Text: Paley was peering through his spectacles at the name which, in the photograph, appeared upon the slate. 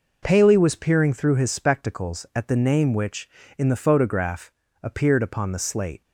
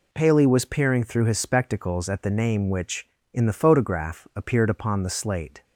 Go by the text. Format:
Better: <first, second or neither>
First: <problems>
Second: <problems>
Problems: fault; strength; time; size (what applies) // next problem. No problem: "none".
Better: neither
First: none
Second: none